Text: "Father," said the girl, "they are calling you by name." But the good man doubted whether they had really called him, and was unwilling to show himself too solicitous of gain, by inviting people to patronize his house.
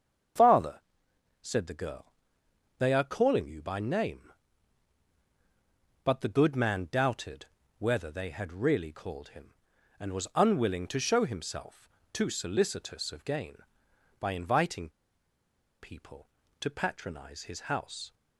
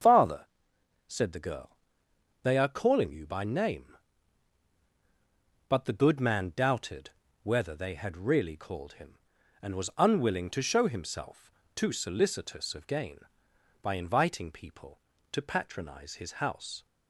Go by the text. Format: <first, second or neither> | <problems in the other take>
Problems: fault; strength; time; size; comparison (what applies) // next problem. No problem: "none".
second | starts louder than the rest; strong; until 1.9 s; 7 dB; strong in the second // pauses between "doubted" and "whether"; slight; at 7.4 s; 0.32 s long; slight in the second // pauses between "himself" and "too"; slight; at 11.8 s; 0.24 s long; slight in the second // pauses between "inviting" and "people"; noticeable; at 14.9 s; 0.91 s long